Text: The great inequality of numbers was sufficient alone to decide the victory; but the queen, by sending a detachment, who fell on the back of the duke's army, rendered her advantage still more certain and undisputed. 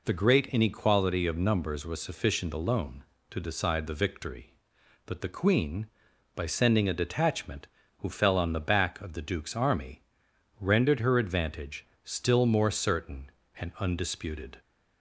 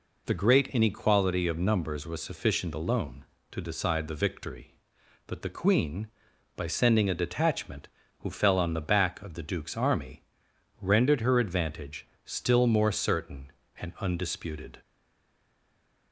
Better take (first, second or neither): first